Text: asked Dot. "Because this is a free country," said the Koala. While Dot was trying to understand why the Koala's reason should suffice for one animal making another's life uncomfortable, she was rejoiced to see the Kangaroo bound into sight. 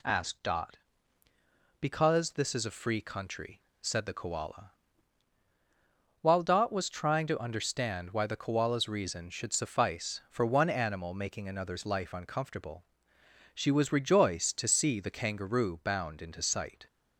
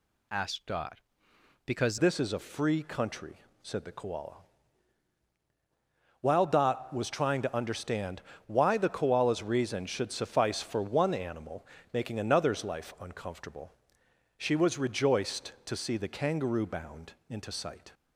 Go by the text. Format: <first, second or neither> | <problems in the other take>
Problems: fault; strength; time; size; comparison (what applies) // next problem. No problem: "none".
first | changes voice at "this"; from 1.9 s on; 16.0 s long // pauses between "understand" and "why"; slight; at 8.2 s; 0.26 s long // pauses between "animal" and "making"; slight; at 11.6 s; 0.28 s long // pauses between "bound" and "into"; slight; at 17.1 s; 0.16 s long